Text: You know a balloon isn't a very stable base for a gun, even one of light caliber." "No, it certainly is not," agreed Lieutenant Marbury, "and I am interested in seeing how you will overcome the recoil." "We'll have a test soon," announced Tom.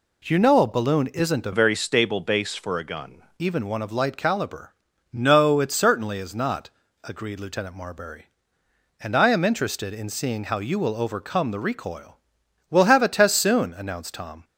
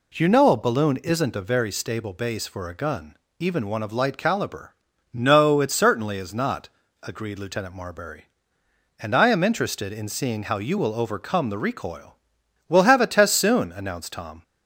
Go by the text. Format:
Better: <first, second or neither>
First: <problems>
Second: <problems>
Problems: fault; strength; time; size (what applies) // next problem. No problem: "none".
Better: second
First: changes voice from "very" to "gun"; from 1.5 to 3.2 s; 1.7 s long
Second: none